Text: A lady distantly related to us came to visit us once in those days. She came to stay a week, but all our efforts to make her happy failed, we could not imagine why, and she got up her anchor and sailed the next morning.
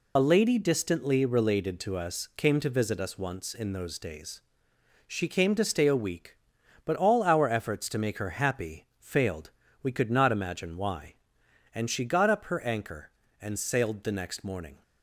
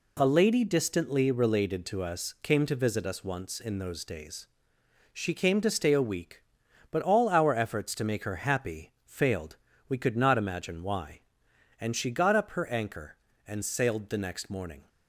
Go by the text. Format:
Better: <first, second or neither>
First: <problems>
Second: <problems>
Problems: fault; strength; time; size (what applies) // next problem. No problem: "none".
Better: second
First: loses the start of "A"; at 0.1 s; 40 ms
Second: none